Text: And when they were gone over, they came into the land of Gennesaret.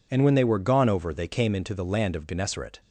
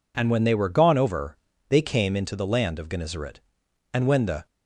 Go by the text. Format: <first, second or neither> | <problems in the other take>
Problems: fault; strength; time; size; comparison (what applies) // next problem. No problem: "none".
first | goes on to say "And when the"; from 3.9 s on; 0.54 s long